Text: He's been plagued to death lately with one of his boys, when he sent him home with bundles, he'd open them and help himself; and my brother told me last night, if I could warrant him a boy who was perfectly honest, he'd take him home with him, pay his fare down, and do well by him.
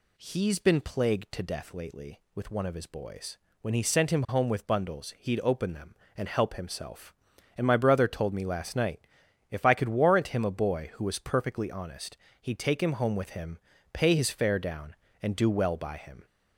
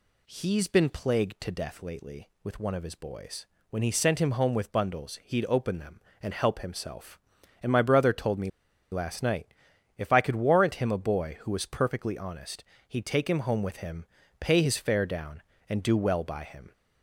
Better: first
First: none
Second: pauses between "me" and "last"; at 8.4 s; 0.42 s long

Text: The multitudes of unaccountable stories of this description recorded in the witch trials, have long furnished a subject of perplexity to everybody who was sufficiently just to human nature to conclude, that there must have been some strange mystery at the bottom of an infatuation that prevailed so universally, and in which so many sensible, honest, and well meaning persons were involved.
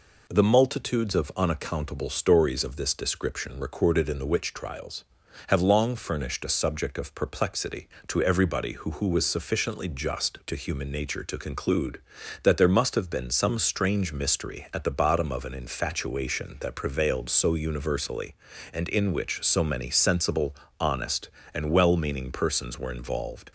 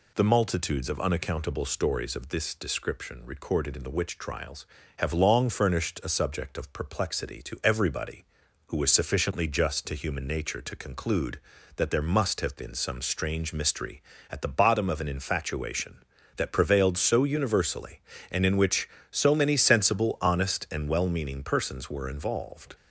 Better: second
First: says "who" twice; at 8.9 s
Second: none

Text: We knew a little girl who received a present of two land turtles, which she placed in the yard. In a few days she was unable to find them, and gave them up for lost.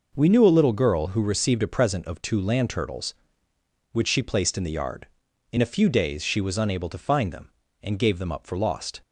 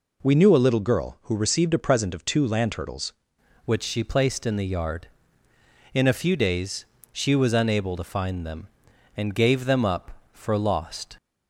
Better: first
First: none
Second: changes voice at "which"; from 3.6 s on; 7.5 s long // pauses between "days" and "she"; slight; at 6.8 s; 0.28 s long

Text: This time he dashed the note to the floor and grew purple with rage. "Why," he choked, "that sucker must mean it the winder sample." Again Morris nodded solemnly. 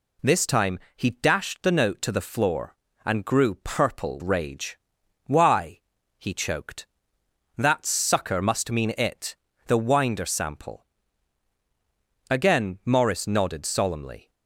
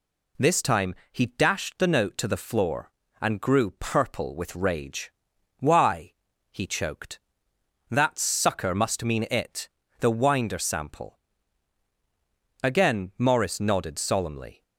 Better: second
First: pauses between "time" and "he"; slight; at 0.7 s; 0.18 s long // skips "with"; at 4.2 s // pauses between "it" and "the"; slight; at 9.3 s; 0.32 s long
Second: pauses between "time" and "he"; slight; at 0.9 s; 0.18 s long // pauses between "it" and "the"; slight; at 9.6 s; 0.32 s long

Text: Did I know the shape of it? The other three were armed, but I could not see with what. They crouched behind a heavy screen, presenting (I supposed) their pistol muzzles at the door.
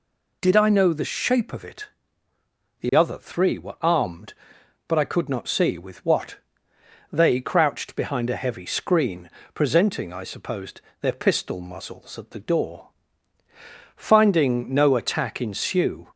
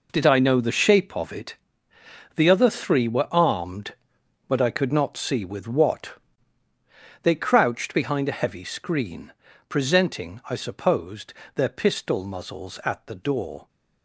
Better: second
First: goes on to say "Finding no attack ensue"; strong; from 13.9 s on; 2.1 s long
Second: none

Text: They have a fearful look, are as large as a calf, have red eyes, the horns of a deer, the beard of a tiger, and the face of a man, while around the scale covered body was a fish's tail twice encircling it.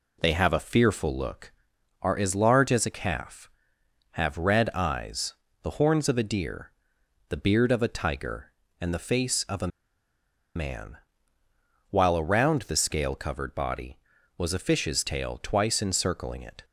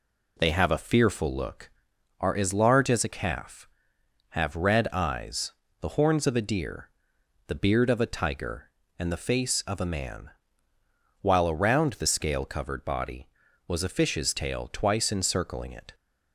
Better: second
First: pauses between "a" and "man"; noticeable; at 9.6 s; 0.88 s long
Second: none

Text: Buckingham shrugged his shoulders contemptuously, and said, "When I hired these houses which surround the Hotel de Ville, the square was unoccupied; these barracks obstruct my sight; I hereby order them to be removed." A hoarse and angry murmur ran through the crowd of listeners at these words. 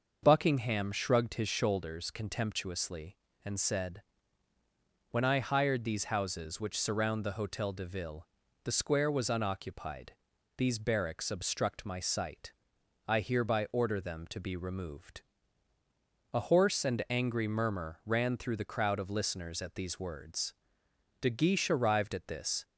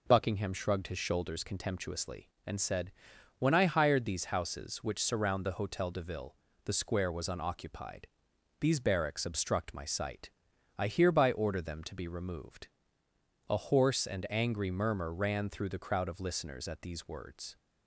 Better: second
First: starts louder than the rest; noticeable; until 1.2 s; 6 dB // goes on to say "De Guiche arrived at this"; from 21.1 s on; 1.4 s long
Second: none

